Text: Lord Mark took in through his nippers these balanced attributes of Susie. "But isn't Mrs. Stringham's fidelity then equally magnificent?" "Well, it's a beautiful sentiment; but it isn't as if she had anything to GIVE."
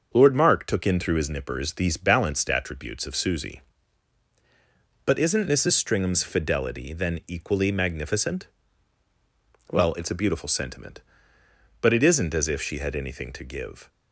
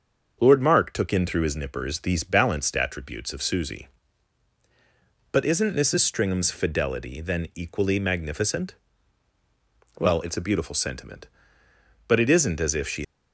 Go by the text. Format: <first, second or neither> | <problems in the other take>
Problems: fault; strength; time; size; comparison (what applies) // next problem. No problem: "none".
first | starts louder than the rest; until 1.4 s; 6.5 dB; also in the first // stops before "had anything to GIVE"; at 13.0 s